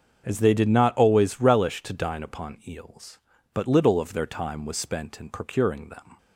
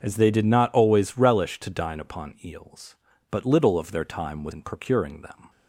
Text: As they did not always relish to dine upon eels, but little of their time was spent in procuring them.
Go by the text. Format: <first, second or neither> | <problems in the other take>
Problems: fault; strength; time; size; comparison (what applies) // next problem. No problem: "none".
first | starts louder than the rest; until 1.0 s; 6.5 dB; also in the first // skips "spent"; at 4.5 s